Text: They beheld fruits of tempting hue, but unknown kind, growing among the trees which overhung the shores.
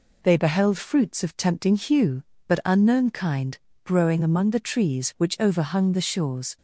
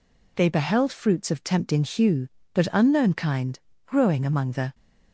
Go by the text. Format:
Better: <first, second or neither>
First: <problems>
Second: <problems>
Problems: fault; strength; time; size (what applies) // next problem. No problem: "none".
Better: first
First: none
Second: stops before "trees which overhung the shores"; at 4.7 s